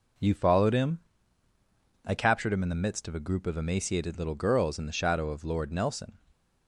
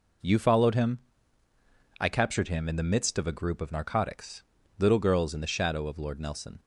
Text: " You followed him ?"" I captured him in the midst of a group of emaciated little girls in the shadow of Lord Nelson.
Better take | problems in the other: first | says "narcotics" for "emaciated"; at 3.7 s

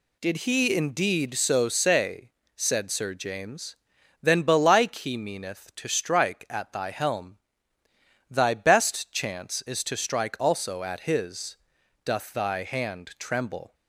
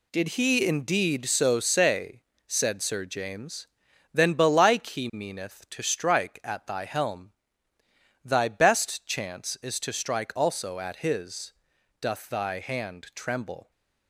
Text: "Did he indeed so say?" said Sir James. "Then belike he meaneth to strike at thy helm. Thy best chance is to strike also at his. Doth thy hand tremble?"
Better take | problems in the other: first | gets quieter; strong; throughout; 7.5 dB

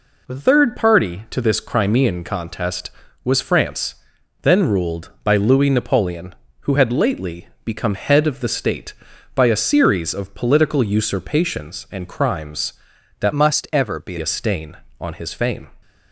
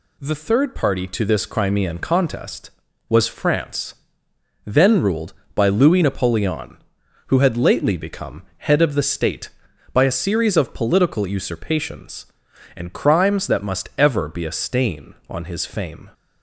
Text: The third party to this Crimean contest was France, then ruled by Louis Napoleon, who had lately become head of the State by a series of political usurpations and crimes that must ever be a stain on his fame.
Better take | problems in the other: second | pauses between "lately" and "become"; slight; at 7.4 s; 0.18 s long // changes voice from "must" to "be"; from 13.3 to 14.1 s; 0.8 s long

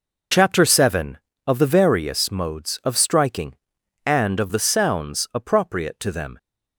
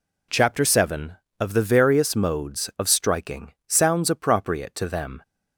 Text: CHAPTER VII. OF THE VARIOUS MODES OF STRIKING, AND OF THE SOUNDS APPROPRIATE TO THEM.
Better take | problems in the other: first | skips "AND OF THE"; at 3.6 s

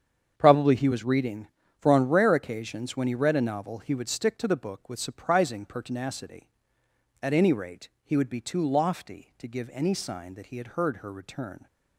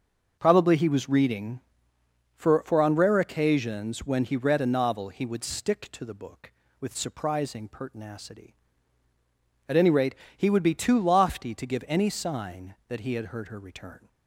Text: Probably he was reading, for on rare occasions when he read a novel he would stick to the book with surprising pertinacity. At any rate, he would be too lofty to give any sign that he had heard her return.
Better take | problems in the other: first | starts louder than the rest; until 1.4 s; 6 dB; strong in the first // says "for" twice; at 2.6 s

